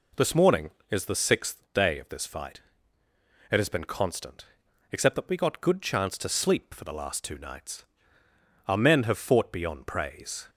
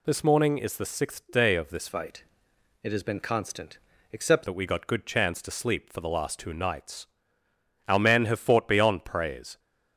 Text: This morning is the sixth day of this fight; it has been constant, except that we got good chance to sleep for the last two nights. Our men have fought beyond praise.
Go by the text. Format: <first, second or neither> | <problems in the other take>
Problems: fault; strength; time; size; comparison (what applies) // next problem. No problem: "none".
first | changes voice from "fight" to "except"; from 1.8 to 4.4 s; 2.6 s long